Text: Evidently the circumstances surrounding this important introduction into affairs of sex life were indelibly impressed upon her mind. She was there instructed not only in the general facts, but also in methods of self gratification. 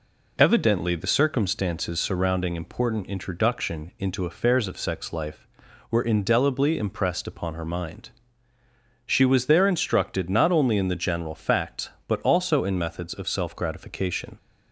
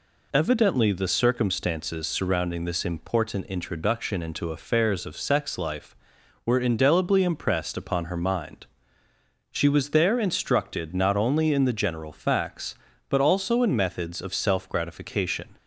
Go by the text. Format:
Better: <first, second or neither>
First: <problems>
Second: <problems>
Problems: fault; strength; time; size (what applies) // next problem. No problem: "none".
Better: second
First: skips "this"; at 2.5 s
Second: none